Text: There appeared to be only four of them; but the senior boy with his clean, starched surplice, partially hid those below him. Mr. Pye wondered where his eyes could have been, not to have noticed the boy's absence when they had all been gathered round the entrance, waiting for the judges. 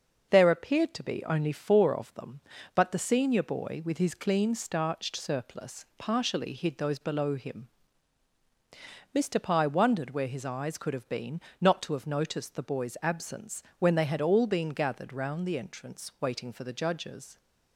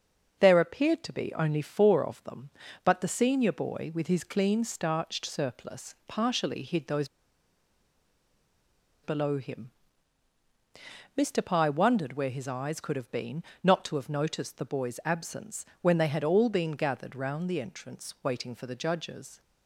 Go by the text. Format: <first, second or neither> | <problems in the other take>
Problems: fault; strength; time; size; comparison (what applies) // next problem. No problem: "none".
first | starts louder than the rest; until 1.4 s; 6 dB; also in the first // pauses between "those" and "below"; strong; at 7.0 s; 1.9 s long // pauses between "absence" and "when"; slight; at 15.6 s; 0.16 s long; slight in the first